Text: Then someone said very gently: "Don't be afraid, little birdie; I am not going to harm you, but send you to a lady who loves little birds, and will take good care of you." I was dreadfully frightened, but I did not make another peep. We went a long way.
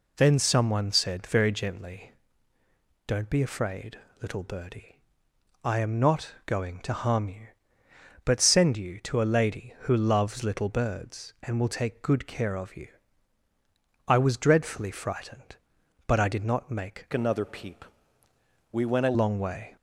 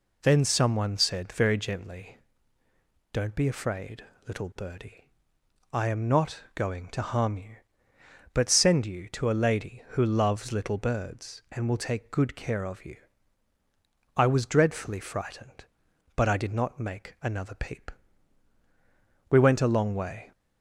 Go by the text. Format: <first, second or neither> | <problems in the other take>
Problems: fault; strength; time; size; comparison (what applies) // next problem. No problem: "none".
second | changes voice from "another" to "a"; from 17.1 to 19.1 s; 2.0 s long